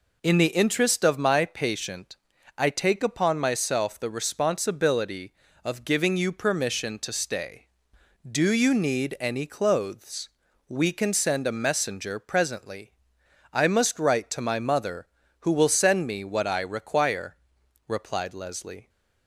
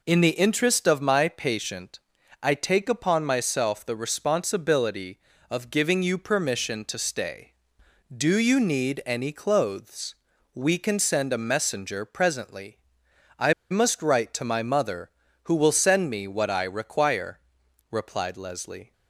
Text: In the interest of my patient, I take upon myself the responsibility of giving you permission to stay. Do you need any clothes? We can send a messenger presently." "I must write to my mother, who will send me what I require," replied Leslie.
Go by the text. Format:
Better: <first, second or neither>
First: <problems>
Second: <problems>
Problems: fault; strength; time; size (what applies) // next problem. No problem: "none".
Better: first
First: none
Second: pauses between "I" and "must"; slight; at 13.5 s; 0.18 s long